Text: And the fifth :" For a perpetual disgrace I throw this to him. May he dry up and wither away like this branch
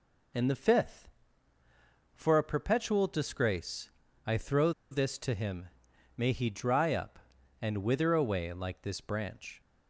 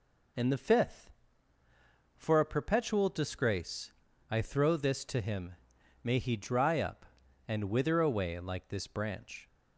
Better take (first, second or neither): second